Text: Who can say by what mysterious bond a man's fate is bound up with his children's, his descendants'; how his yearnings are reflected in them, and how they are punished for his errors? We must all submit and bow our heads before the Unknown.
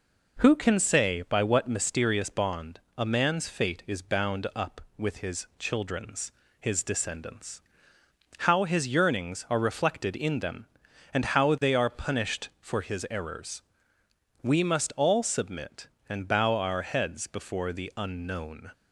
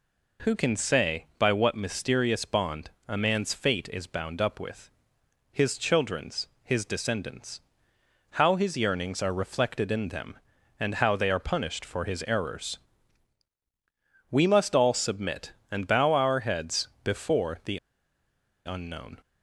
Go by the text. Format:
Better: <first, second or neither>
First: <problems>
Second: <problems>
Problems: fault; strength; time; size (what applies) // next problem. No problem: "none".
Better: first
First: pauses between "bond" and "a"; slight; at 2.7 s; 0.16 s long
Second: pauses between "bond" and "a"; slight; at 2.8 s; 0.18 s long // pauses between "with" and "his"; noticeable; at 4.8 s; 0.62 s long // pauses between "heads" and "before"; slight; at 16.8 s; 0.16 s long // pauses between "the" and "Unknown"; noticeable; at 17.7 s; 0.88 s long